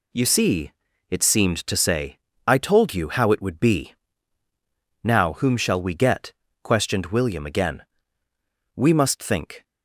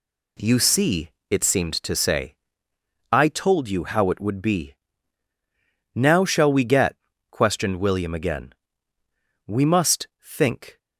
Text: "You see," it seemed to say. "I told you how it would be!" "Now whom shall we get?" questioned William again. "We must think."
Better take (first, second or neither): first